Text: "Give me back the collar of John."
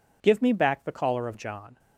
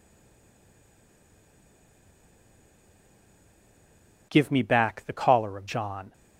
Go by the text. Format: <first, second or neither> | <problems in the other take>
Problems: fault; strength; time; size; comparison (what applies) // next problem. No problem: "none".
first | stays silent before the first word; strong; until 4.3 s; 4.3 s long